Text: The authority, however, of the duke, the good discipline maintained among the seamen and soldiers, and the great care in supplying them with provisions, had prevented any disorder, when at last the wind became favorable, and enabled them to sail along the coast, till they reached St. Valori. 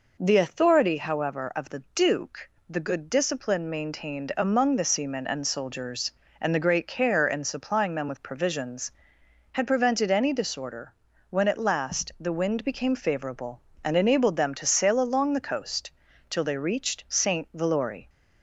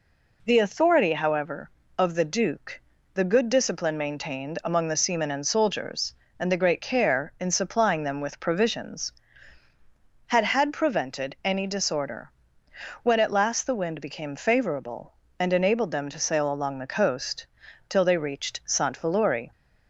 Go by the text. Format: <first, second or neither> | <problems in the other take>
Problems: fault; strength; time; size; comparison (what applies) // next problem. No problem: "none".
first | says "had" twice; at 10.4 s